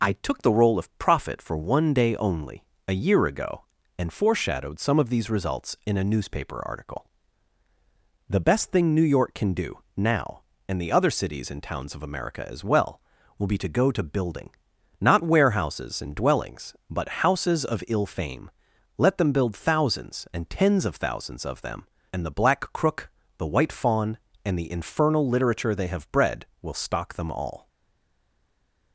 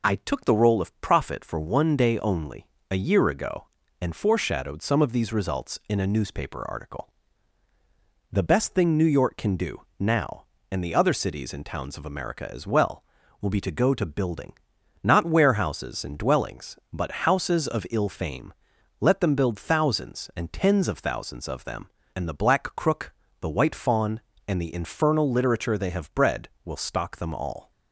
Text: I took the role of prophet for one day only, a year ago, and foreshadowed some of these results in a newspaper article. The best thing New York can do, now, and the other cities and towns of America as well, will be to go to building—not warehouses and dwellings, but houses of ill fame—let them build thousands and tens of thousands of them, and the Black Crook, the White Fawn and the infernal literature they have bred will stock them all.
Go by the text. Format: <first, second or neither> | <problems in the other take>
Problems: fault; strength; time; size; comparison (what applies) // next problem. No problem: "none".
second | stays silent after the last word; noticeable; from 27.6 s on; 1.3 s long